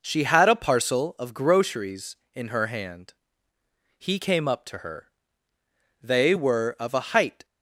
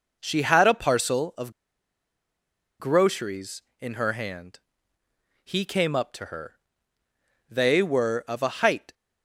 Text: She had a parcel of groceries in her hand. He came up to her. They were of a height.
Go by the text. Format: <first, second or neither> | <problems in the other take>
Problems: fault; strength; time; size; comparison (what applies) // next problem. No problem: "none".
first | pauses between "of" and "groceries"; strong; at 1.5 s; 1.2 s long